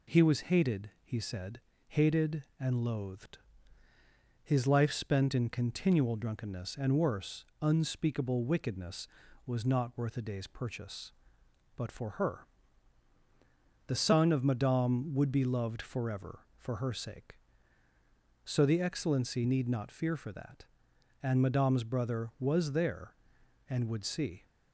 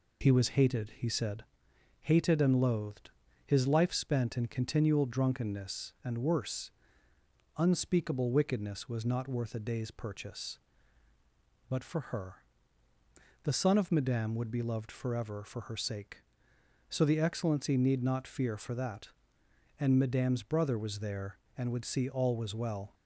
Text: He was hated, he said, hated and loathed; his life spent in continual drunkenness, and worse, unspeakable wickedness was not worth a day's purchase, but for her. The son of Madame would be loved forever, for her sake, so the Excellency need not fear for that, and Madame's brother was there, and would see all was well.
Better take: second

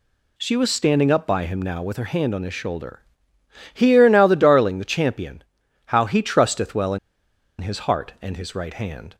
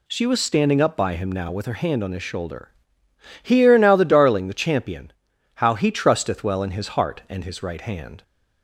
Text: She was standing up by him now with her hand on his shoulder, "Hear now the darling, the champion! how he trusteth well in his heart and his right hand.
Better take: second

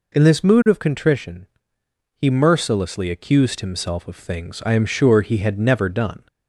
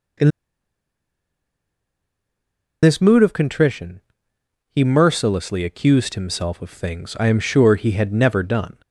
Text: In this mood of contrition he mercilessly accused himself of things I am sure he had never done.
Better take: first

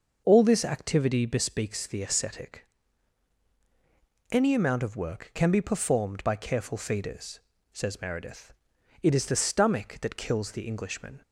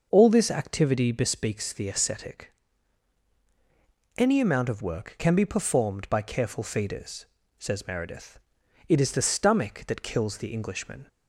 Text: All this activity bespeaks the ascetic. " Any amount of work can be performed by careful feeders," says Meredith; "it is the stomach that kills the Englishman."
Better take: neither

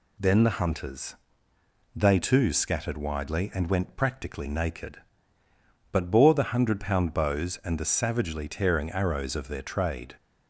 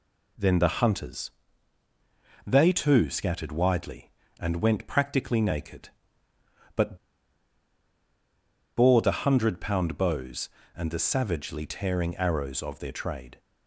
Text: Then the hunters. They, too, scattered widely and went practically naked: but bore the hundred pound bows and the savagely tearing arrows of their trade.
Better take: first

